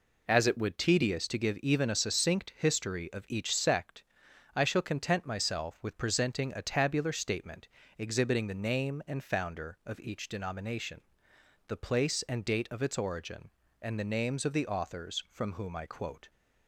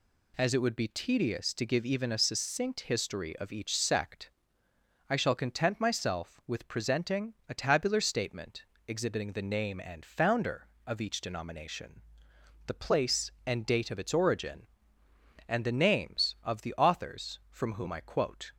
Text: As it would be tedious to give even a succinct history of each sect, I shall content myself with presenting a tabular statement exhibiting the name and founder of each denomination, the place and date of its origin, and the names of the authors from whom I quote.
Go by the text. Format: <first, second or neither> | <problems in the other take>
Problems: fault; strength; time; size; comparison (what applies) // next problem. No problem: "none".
second | skips "be"; at 0.7 s // pauses between "statement" and "exhibiting"; slight; at 7.6 s; 0.30 s long; slight in the second